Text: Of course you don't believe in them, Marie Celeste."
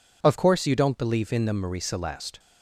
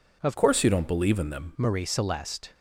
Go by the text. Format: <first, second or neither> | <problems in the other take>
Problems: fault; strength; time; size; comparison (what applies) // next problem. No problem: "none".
first | changes voice from "course" to "them"; from 0.3 to 1.5 s; 1.2 s long